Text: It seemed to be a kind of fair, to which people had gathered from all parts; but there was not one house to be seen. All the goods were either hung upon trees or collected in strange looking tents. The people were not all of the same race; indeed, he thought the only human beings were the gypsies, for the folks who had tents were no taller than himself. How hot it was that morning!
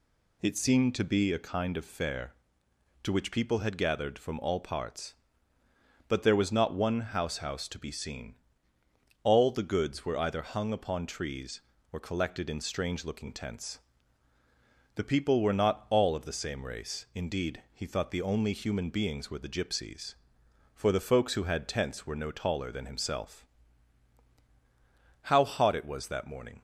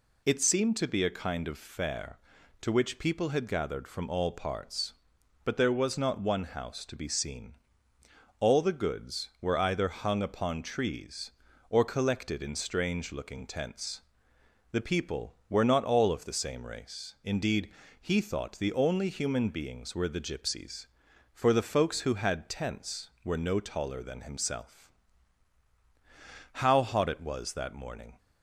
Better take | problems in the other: second | says "house" twice; at 7.3 s

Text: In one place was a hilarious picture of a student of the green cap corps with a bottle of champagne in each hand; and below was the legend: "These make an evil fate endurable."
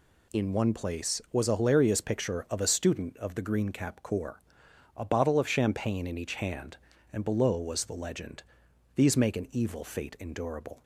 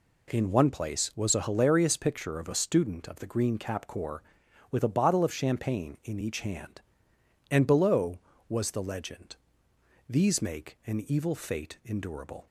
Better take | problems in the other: second | skips "with"; at 4.6 s

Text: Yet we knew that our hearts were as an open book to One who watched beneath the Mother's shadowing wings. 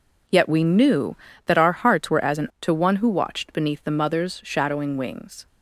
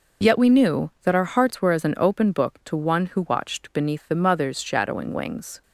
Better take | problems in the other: second | skips "open book"; at 2.5 s

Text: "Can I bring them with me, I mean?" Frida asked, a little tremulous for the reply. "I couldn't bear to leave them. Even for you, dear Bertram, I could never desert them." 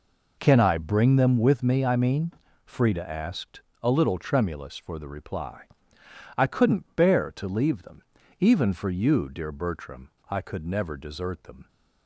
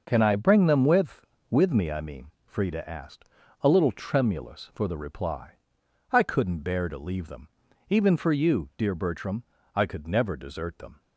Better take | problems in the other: first | says "with" twice; at 1.5 s

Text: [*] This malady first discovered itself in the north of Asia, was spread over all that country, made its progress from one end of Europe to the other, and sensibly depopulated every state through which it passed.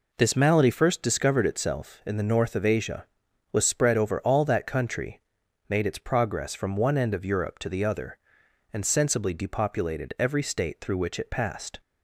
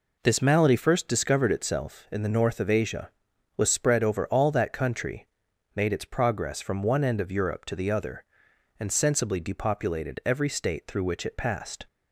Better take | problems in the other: neither | none

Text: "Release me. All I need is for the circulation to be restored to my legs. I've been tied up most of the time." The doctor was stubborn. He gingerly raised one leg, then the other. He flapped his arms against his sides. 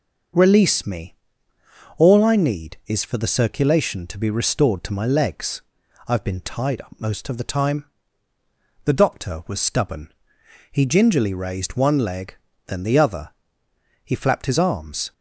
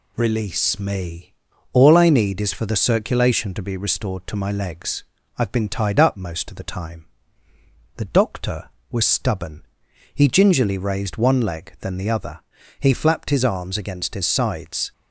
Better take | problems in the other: second | starts louder than the rest; noticeable; until 2.1 s; 6 dB // stops before "against his sides"; at 15.1 s

